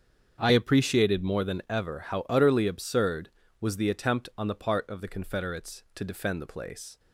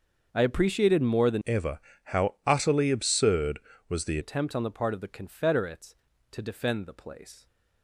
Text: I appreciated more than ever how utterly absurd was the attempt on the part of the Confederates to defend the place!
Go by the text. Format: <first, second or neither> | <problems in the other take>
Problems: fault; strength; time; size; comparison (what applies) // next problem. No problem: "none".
first | starts louder than the rest; until 1.3 s; 6.5 dB; strong in the first // changes voice from "ever" to "the"; from 1.4 to 4.1 s; 2.7 s long // pauses between "ever" and "how"; slight; at 1.7 s; 0.26 s long